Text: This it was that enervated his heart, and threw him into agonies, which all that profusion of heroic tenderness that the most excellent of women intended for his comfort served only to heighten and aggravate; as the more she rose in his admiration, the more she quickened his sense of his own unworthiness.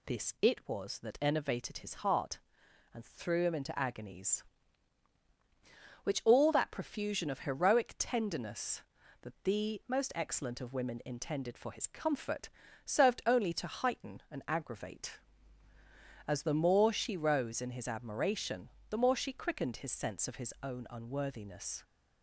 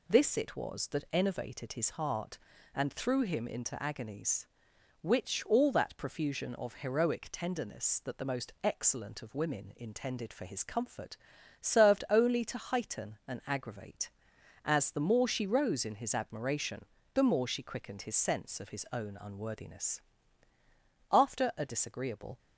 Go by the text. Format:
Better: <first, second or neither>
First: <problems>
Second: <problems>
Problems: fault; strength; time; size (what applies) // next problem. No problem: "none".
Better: first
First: pauses between "comfort" and "served"; slight; at 12.4 s; 0.36 s long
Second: pauses between "comfort" and "served"; at 11.1 s; 0.44 s long // goes on to say "After a disagreeable"; noticeable; from 21.0 s on; 1.2 s long